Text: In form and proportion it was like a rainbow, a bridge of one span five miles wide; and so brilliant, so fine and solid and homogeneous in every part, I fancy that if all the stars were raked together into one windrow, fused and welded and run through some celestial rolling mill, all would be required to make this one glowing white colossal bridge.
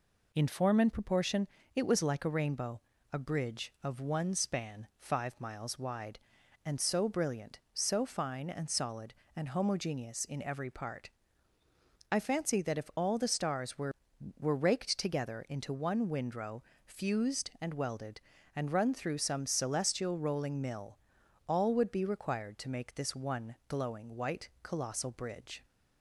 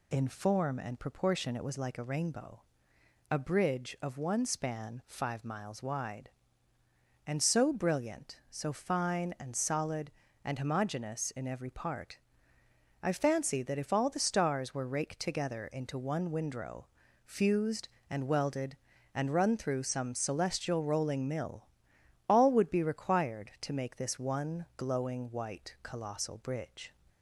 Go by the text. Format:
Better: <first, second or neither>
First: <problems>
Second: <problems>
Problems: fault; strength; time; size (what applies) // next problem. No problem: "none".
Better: second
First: pauses between "proportion" and "it"; slight; at 1.4 s; 0.26 s long // says "were" twice; at 14.3 s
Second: none